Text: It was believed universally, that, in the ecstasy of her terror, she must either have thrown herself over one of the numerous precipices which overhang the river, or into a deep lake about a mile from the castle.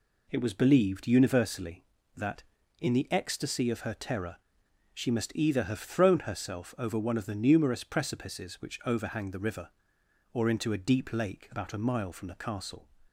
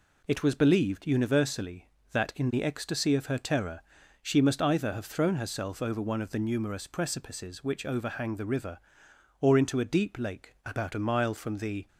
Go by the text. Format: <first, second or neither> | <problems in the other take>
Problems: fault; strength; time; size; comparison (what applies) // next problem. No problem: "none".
first | stops before "castle"; at 11.8 s